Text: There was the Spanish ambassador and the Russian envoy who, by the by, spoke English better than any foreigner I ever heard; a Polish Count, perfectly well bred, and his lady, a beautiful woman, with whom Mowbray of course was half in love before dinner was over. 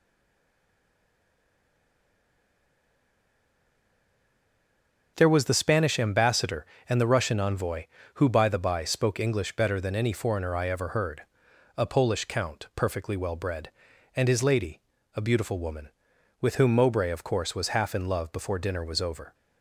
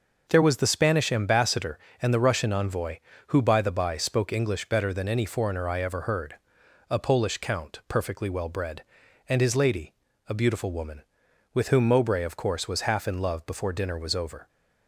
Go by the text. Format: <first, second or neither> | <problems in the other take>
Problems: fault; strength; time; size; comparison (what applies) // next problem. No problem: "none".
second | stays silent before the first word; strong; until 5.1 s; 5.1 s long